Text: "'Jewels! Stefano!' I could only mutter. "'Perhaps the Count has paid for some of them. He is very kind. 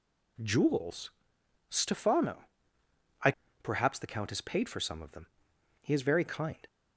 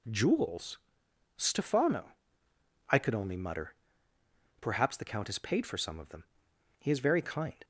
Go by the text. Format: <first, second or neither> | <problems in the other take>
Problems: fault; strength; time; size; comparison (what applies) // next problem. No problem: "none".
second | skips "could only mutter"; at 3.4 s